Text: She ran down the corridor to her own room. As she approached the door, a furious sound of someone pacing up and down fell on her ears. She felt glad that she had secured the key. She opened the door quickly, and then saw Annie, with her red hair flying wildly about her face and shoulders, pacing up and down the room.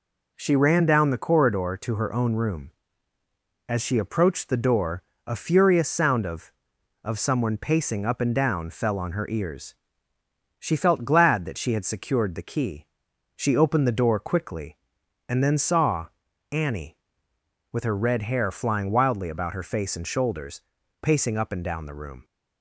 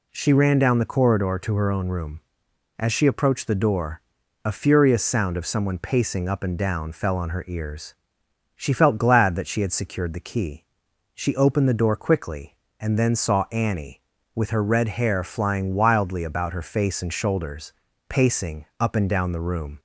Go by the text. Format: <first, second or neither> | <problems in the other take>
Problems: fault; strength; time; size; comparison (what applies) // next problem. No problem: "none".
second | says "of" twice; at 7.0 s // pauses between "saw" and "Annie"; at 16.0 s; 0.44 s long